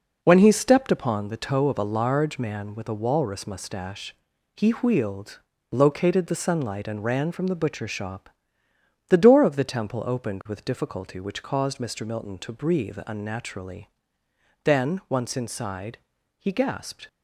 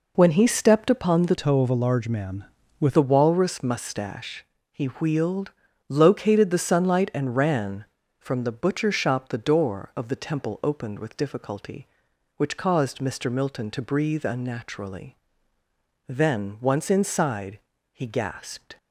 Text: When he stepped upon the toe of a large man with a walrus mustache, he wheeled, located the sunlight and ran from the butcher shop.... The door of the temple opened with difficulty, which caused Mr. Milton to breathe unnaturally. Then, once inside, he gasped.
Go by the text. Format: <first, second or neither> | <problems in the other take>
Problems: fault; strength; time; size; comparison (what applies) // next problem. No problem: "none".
first | changes voice from "toe" to "with"; from 1.3 to 2.9 s; 1.6 s long